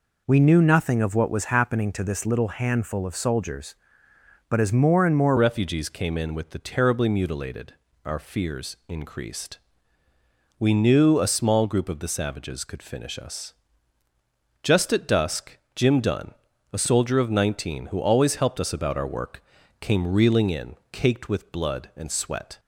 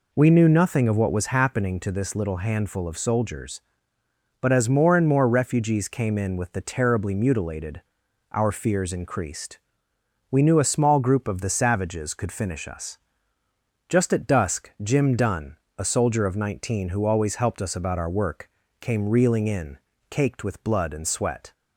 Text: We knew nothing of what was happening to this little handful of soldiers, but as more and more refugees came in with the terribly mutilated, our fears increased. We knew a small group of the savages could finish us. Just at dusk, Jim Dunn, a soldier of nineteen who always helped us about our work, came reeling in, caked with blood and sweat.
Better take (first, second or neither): second